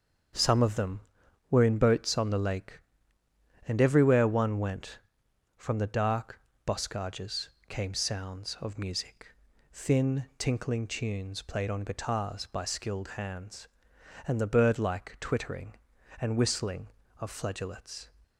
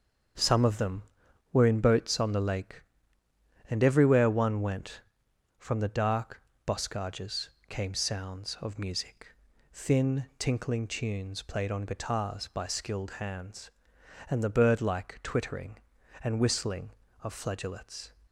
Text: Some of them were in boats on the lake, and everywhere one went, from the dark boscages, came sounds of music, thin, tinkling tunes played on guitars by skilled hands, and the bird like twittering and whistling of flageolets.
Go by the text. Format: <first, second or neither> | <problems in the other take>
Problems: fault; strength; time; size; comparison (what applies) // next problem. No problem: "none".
neither | starts louder than the rest; the same in both // pauses between "dark" and "boscages"; slight; the same in both